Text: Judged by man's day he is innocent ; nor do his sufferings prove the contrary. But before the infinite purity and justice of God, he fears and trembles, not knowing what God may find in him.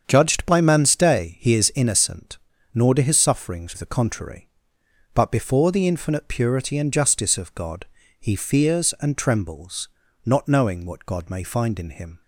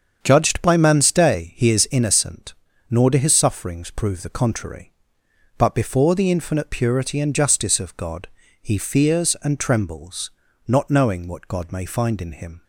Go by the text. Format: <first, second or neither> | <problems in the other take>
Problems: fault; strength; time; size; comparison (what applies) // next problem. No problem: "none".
second | starts louder than the rest; until 1.0 s; 7 dB; strong in the second // skips "prove"; at 3.7 s